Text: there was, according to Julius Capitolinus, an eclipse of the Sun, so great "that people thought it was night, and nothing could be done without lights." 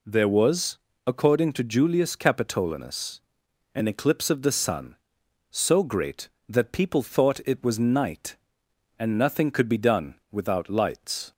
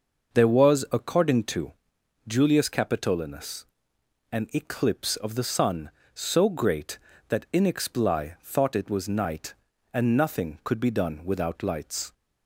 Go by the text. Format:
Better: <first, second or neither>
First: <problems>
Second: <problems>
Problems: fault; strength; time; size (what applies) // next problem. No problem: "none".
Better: first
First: none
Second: pauses between "to" and "Julius"; noticeable; at 1.7 s; 0.52 s long // says "inexpli" for "people"; at 7.5 s